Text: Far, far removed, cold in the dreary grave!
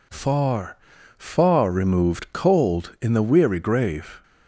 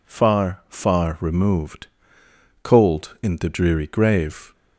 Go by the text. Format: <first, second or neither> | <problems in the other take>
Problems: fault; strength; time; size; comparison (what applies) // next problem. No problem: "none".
second | says "weary" for "dreary"; at 3.2 s